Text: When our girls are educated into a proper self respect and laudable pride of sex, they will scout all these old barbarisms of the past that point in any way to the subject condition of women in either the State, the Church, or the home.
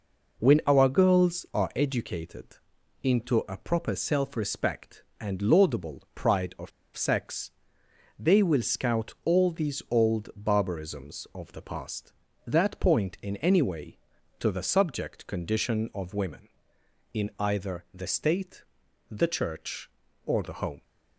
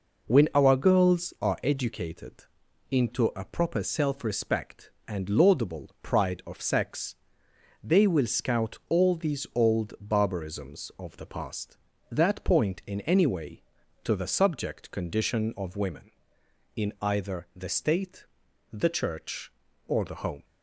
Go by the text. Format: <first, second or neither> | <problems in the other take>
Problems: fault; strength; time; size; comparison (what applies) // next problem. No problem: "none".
second | pauses between "educated" and "into"; noticeable; at 2.5 s; 0.46 s long; noticeable in the second // pauses between "of" and "sex"; slight; at 6.7 s; 0.25 s long